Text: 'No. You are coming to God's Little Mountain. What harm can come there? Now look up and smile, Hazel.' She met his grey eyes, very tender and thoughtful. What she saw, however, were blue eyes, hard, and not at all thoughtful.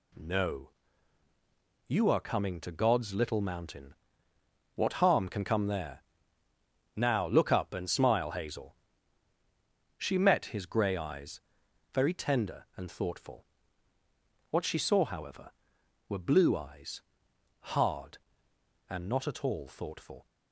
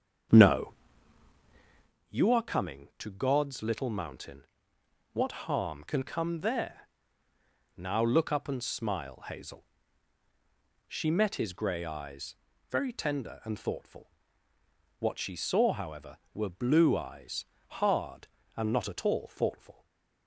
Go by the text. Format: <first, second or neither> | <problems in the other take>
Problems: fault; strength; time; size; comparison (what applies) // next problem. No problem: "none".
first | starts louder than the rest; strong; until 1.9 s; 7.5 dB // stays silent after the last word; slight; from 19.7 s on; 0.5 s long